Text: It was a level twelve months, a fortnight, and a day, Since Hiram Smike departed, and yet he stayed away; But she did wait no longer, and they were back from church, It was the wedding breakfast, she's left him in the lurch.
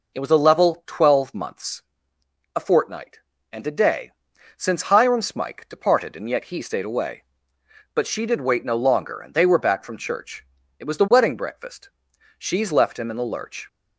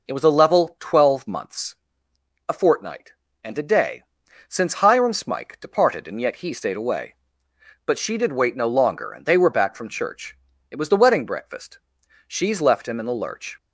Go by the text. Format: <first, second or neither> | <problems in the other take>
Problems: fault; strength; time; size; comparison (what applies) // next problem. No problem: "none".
neither | none